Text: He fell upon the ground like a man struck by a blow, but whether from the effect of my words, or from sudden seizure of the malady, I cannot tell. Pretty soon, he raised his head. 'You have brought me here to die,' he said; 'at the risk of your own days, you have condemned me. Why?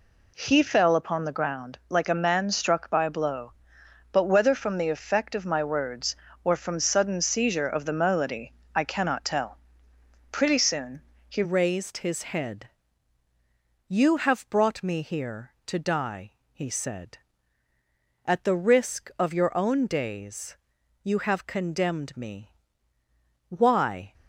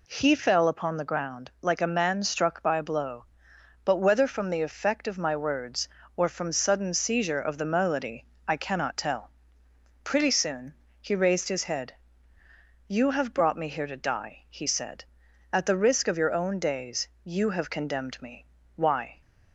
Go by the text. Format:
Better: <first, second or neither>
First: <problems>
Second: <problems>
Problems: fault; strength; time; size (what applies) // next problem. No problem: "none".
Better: second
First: changes voice at "raised"; from 11.4 s on; 12.7 s long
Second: none